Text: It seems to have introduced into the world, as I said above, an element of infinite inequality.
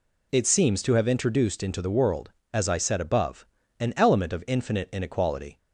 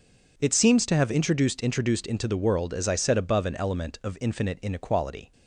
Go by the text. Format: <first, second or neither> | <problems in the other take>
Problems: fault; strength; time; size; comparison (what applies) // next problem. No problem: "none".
first | says "introduced" twice; at 1.6 s